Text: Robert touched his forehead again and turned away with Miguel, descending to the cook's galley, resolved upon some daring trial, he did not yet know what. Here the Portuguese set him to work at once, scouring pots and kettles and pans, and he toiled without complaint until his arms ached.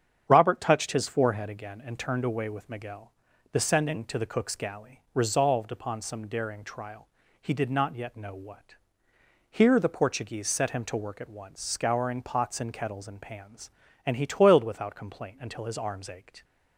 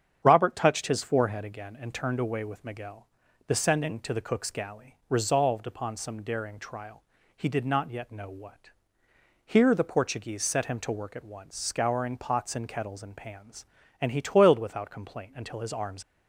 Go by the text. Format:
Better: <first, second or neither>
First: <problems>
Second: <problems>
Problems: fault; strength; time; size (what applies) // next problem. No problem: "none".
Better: first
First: starts louder than the rest; strong; until 1.3 s; 8 dB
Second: starts louder than the rest; strong; until 1.2 s; 8 dB // stops before "ached"; at 16.0 s